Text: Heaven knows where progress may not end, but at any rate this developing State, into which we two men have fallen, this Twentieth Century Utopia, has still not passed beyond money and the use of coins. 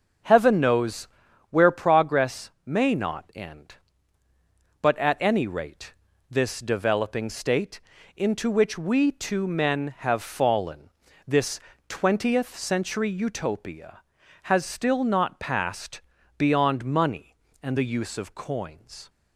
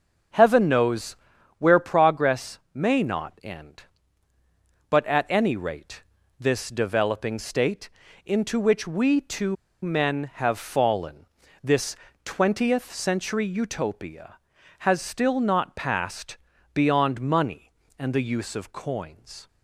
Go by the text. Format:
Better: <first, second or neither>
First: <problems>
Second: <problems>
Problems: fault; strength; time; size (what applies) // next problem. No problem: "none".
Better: first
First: starts louder than the rest; until 1.6 s; 7 dB // pauses between "knows" and "where"; at 1.0 s; 0.44 s long // pauses between "rate" and "this"; at 5.9 s; 0.38 s long // pauses between "this" and "Twentieth"; slight; at 11.5 s; 0.30 s long // pauses between "passed" and "beyond"; at 15.9 s; 0.38 s long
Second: starts louder than the rest; until 1.7 s; 7 dB // pauses between "knows" and "where"; at 1.1 s; 0.44 s long // pauses between "rate" and "this"; at 6.0 s; 0.38 s long // pauses between "two" and "men"; slight; at 9.5 s; 0.29 s long // pauses between "this" and "Twentieth"; slight; at 11.9 s; 0.30 s long // pauses between "passed" and "beyond"; at 16.3 s; 0.38 s long